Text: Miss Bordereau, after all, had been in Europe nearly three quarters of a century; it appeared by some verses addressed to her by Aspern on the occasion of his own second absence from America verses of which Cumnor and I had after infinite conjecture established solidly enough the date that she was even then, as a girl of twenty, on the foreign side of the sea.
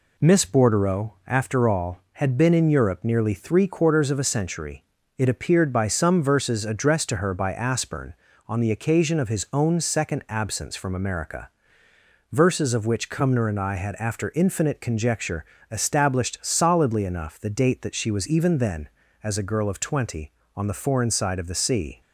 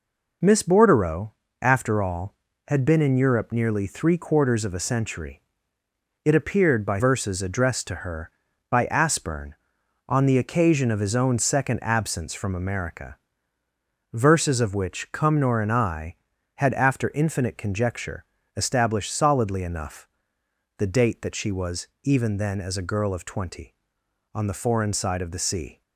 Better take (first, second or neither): first